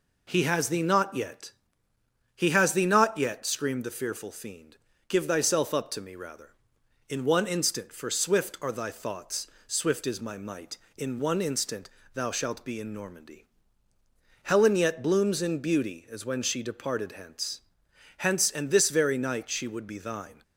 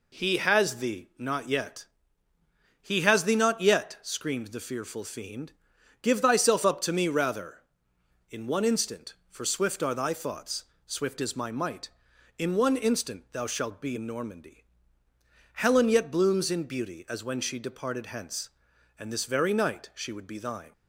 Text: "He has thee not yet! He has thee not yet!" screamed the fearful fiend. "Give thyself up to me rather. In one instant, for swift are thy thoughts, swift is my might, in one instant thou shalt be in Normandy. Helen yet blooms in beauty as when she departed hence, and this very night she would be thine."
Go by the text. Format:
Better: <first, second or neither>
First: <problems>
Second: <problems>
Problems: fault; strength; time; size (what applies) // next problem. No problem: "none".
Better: second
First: pauses between "instant" and "thou"; slight; at 11.8 s; 0.24 s long // says "hence" twice; at 18.1 s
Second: none